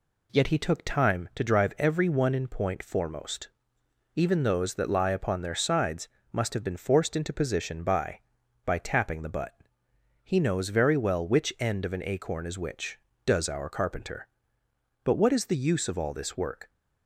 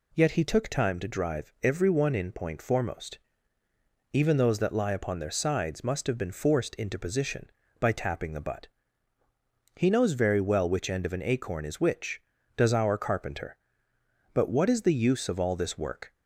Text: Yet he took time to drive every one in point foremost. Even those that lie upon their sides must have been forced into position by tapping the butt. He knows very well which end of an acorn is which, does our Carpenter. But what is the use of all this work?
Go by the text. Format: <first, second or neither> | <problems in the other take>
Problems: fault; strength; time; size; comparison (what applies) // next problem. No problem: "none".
second | pauses between "sides" and "must"; slight; at 6.0 s; 0.24 s long // says "by" twice; at 8.6 s